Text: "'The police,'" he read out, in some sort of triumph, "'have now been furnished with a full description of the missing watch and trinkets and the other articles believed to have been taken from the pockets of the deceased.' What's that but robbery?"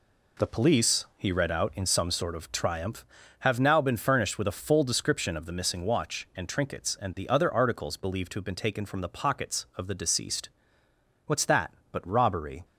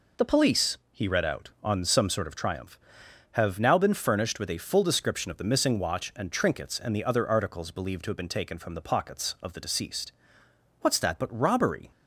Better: first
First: none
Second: says "on" for "in"; at 1.6 s

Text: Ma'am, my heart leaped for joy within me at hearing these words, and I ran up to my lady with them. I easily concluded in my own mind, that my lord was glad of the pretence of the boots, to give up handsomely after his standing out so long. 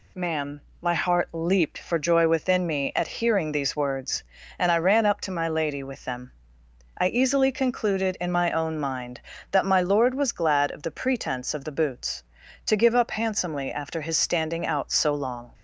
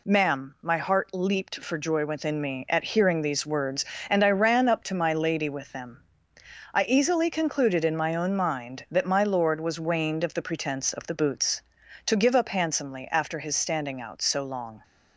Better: first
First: none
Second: says "waned" for "glad"; at 9.7 s

